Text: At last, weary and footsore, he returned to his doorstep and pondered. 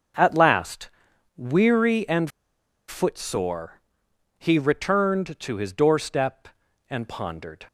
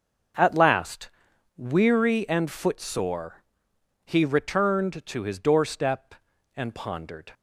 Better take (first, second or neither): second